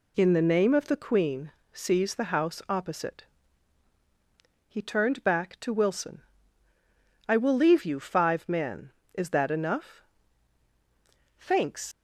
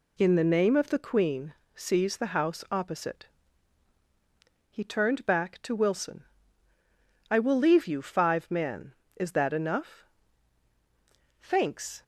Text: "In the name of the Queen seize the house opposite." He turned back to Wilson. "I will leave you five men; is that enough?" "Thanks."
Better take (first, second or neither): second